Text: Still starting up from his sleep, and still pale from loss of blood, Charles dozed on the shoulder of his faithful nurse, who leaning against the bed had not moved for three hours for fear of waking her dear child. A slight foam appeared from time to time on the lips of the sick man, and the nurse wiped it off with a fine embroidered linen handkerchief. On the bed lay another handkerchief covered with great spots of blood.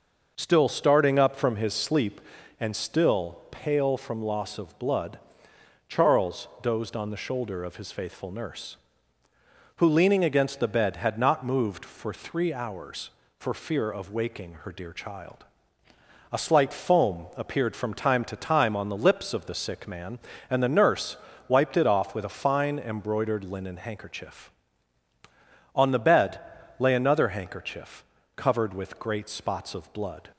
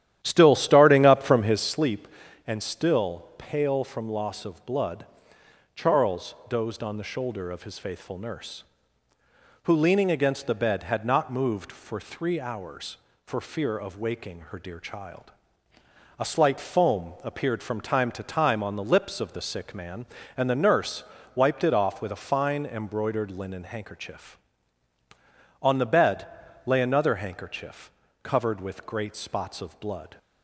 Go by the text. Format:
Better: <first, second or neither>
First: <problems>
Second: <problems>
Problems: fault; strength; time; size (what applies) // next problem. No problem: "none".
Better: first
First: pauses between "nurse" and "wiped"; slight; at 21.1 s; 0.32 s long // pauses between "bed" and "lay"; at 26.3 s; 0.38 s long // pauses between "handkerchief" and "covered"; slight; at 28.0 s; 0.34 s long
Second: starts louder than the rest; strong; until 1.7 s; 11.5 dB // pauses between "nurse" and "wiped"; slight; at 21.0 s; 0.32 s long // pauses between "bed" and "lay"; at 26.2 s; 0.38 s long // pauses between "handkerchief" and "covered"; slight; at 27.8 s; 0.34 s long